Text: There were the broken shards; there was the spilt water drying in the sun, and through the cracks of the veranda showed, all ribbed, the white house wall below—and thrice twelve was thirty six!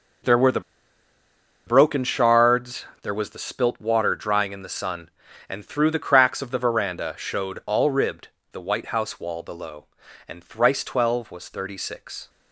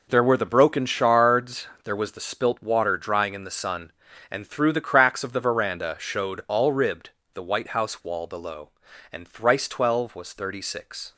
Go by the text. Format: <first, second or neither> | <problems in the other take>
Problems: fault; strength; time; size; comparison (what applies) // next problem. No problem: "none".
second | pauses between "the" and "broken"; at 0.6 s; 1.0 s long